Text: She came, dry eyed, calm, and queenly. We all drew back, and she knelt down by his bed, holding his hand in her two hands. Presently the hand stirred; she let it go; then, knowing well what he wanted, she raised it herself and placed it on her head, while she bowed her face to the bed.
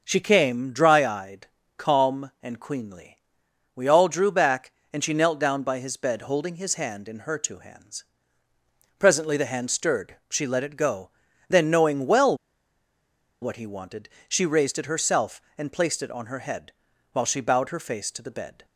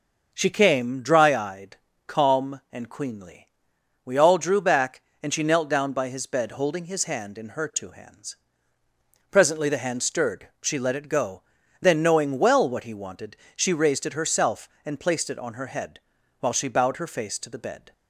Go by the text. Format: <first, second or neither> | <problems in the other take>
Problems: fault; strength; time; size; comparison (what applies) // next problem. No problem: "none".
second | starts louder than the rest; noticeable; until 1.0 s; 6 dB; noticeable in the second // pauses between "well" and "what"; at 12.3 s; 1.0 s long